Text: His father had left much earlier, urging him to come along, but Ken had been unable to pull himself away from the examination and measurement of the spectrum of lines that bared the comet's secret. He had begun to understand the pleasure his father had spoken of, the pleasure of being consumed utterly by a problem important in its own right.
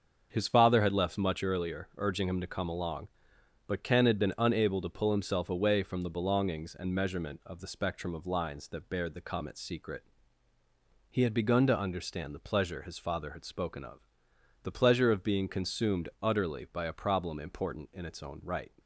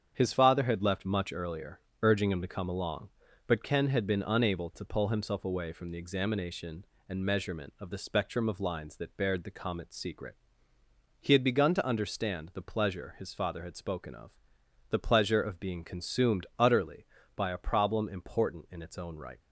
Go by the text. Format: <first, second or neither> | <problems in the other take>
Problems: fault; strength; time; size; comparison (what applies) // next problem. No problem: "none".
second | starts louder than the rest; until 1.3 s; 7 dB; strong in the second // says "belongings" for "examination"; at 6.0 s